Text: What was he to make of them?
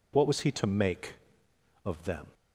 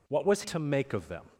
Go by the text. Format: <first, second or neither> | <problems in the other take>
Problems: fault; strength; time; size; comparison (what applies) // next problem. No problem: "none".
first | skips "he"; at 0.4 s